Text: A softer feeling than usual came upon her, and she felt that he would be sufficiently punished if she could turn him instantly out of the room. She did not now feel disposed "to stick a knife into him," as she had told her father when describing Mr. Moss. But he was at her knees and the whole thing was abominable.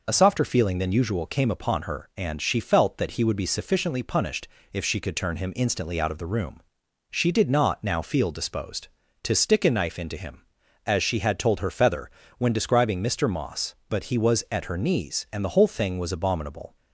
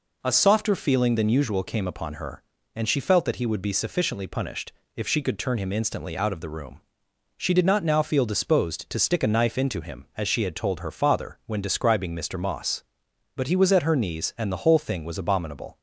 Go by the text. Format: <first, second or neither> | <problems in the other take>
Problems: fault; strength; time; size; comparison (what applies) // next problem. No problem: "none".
second | pauses between "punished" and "if"; slight; at 4.4 s; 0.24 s long; slight in the second // says "feather" for "father"; at 11.7 s